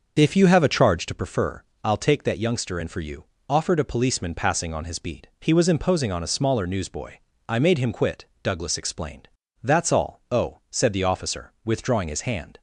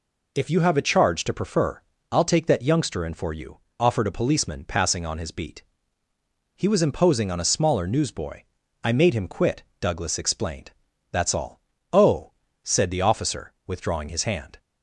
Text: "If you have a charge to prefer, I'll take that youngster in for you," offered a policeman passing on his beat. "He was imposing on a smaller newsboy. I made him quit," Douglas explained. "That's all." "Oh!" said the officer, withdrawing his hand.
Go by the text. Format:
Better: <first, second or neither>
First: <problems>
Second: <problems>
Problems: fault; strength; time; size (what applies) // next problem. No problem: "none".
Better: second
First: starts louder than the rest; until 1.2 s; 6.5 dB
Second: none